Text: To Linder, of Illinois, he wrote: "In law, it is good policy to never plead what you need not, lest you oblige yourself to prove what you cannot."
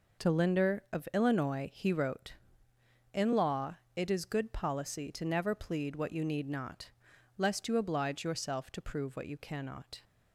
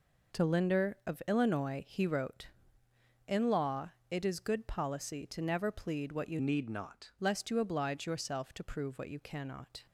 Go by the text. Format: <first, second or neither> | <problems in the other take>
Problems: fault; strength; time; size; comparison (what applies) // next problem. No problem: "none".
first | changes voice from "need" to "not"; from 6.3 to 7.1 s; 0.8 s long